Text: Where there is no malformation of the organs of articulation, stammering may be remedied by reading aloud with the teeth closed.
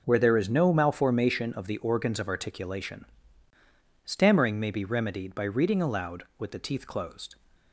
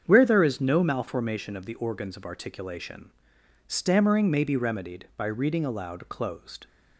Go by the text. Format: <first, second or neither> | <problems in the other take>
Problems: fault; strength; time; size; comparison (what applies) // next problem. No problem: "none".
first | starts louder than the rest; strong; until 1.0 s; 7.5 dB // skips "with the teeth"; at 6.0 s